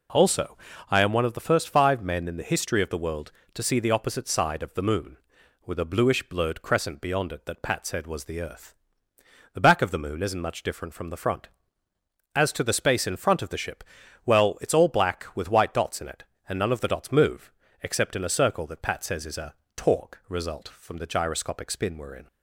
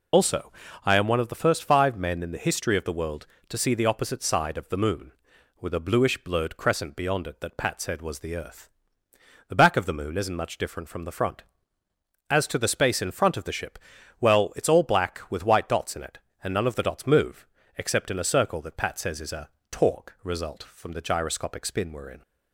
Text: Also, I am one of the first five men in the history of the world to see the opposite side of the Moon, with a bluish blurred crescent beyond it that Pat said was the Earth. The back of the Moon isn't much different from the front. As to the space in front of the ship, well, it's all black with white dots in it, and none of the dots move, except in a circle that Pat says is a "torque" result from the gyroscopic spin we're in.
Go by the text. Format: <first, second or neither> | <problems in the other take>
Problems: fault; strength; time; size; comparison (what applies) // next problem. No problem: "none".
first | loses the start of "Also"; at 0.1 s; 85 ms // pauses between "a" and "torque"; slight; at 19.4 s; 0.24 s long; slight in the first